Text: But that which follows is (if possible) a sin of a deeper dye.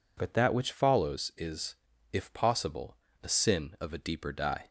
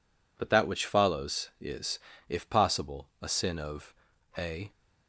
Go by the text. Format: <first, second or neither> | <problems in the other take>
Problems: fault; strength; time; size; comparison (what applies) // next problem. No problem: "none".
first | pauses between "of" and "a"; at 3.9 s; 0.44 s long // stops before "deeper dye"; at 4.7 s